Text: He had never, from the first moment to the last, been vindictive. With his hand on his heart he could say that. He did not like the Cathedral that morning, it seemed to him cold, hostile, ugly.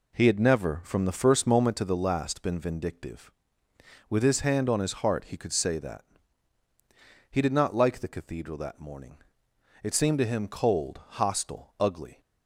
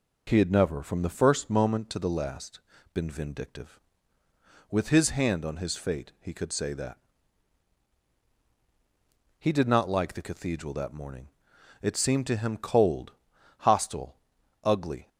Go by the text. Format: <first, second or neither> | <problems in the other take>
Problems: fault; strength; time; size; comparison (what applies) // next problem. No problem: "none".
first | says "fate" for "heart"; at 5.7 s